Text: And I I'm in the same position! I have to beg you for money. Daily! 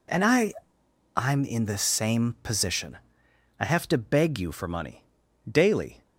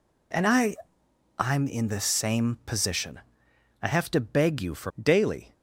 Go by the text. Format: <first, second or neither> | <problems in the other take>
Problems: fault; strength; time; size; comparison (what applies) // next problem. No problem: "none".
first | pauses between "I" and "I'm"; noticeable; at 0.7 s; 0.64 s long; noticeable in the first // skips "money"; at 4.9 s